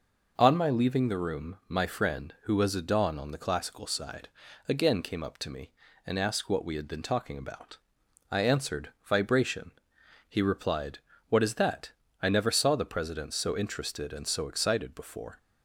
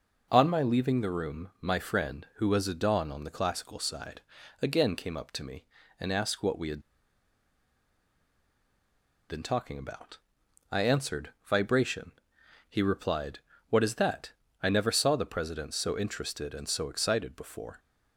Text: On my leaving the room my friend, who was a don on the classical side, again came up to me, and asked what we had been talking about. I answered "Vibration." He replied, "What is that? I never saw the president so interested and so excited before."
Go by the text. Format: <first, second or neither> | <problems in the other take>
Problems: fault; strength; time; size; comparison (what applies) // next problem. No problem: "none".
first | pauses between "had" and "been"; strong; at 6.8 s; 2.4 s long // pauses between "answered" and "Vibration"; slight; at 11.2 s; 0.16 s long; slight in the first